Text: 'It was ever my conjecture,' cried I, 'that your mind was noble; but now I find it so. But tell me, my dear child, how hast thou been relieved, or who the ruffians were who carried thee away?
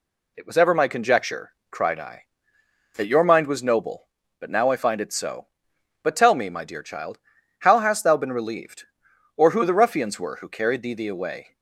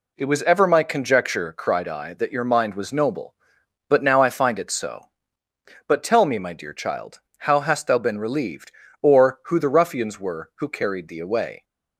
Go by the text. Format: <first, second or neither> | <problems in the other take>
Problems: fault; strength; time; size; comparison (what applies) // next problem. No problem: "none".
second | says "thee" twice; at 10.9 s